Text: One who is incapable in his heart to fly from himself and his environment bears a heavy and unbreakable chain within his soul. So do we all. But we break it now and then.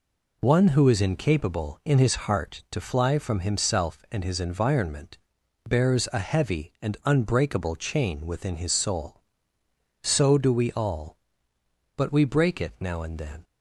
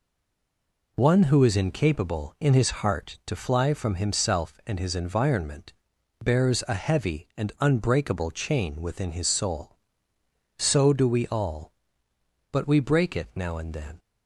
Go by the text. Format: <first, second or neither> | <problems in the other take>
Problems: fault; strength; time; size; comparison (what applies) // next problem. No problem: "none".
first | stays silent before the first word; slight; until 0.9 s; 0.9 s long // pauses between "environment" and "bears"; noticeable; at 5.7 s; 0.50 s long; noticeable in the first